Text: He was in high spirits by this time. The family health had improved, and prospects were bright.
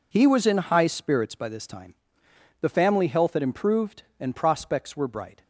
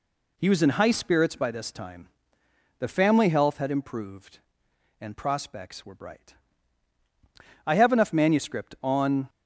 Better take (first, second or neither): first